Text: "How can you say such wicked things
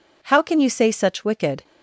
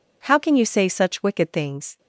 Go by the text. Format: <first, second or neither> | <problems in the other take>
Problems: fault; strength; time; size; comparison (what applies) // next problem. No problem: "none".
second | stops before "things"; at 1.6 s